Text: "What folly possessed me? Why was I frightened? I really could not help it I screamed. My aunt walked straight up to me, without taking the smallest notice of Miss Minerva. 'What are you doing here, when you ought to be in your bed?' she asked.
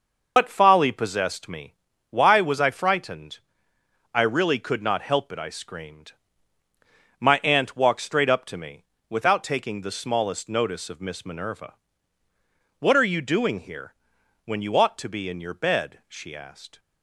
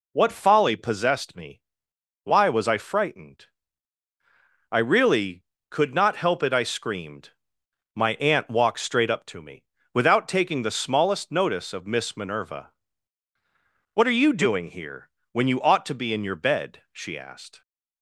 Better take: second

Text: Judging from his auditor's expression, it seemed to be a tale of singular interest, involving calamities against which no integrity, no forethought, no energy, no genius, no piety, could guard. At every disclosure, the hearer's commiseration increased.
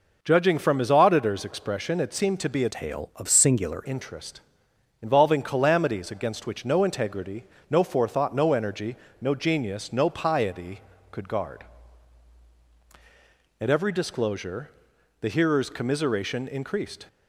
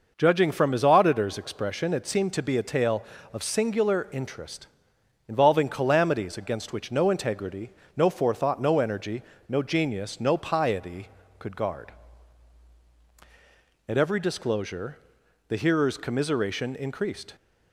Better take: second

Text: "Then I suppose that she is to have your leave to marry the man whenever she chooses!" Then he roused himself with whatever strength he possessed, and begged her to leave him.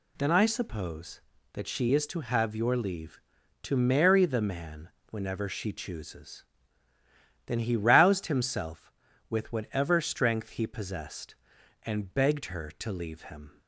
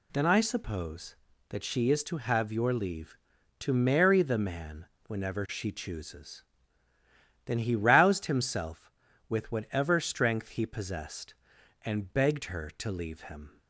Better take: neither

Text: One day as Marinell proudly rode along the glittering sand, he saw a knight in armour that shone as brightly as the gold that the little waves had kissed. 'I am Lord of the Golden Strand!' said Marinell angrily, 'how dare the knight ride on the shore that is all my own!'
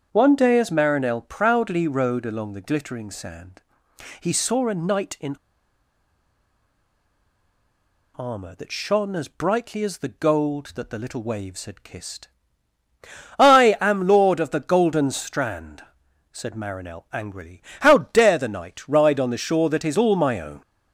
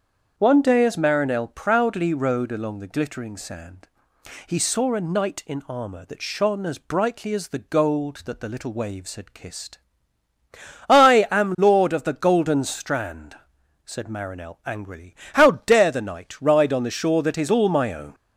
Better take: second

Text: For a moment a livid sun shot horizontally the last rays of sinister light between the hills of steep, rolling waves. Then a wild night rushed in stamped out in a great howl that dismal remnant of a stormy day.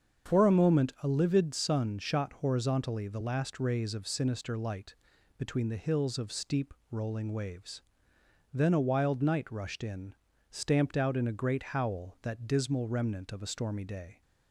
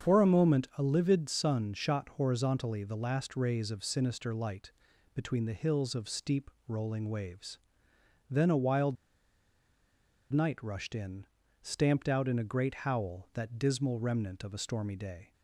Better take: first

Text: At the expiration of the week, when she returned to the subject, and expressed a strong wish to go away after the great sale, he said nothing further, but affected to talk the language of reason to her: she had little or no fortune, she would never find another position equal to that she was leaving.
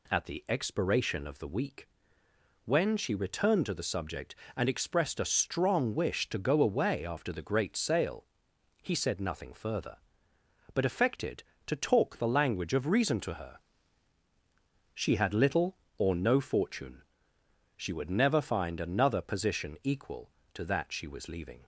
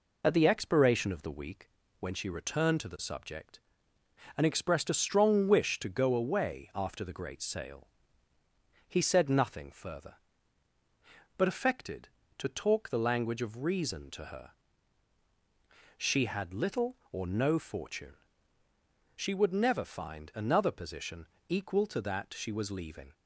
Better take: first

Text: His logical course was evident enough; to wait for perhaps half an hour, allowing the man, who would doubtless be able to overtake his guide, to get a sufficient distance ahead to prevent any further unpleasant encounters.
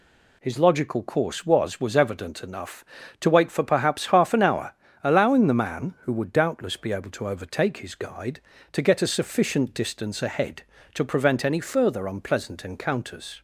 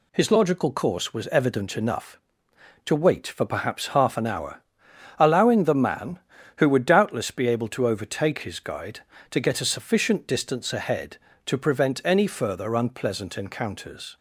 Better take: second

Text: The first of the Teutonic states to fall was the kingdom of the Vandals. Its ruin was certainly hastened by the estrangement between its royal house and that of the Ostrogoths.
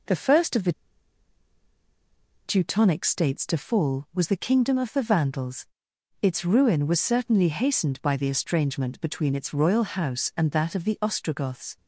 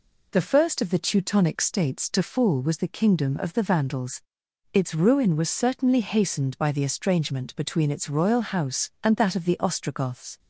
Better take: second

